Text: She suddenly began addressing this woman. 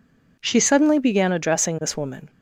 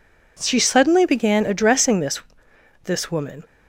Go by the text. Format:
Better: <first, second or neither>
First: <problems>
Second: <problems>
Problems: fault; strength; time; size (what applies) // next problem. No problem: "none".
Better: first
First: none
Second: says "this" twice; at 2.8 s